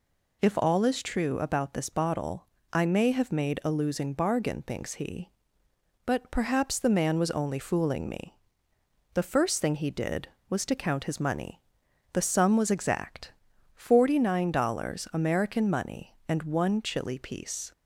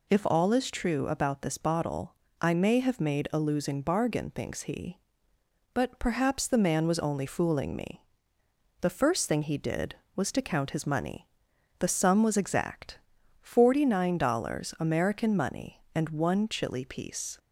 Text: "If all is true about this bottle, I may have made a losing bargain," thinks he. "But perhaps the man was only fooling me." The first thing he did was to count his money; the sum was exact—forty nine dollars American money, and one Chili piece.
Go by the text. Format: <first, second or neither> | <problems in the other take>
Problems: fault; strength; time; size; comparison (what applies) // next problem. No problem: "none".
neither | none